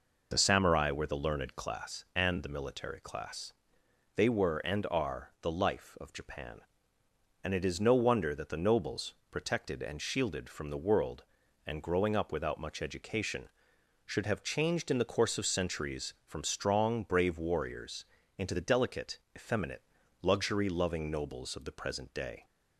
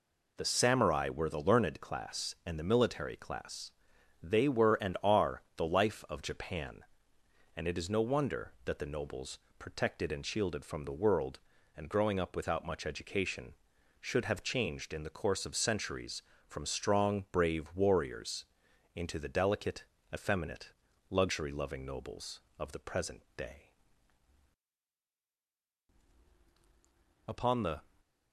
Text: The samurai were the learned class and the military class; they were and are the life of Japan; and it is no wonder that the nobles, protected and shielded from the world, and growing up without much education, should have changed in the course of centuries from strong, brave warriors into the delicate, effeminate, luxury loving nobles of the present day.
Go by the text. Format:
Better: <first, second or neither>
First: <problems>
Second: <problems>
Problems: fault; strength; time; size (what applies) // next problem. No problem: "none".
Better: first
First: pauses between "warriors" and "into"; slight; at 18.0 s; 0.32 s long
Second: pauses between "warriors" and "into"; noticeable; at 18.4 s; 0.48 s long // pauses between "present" and "day"; slight; at 23.2 s; 0.16 s long // goes on to say "Upon the"; from 27.2 s on; 0.54 s long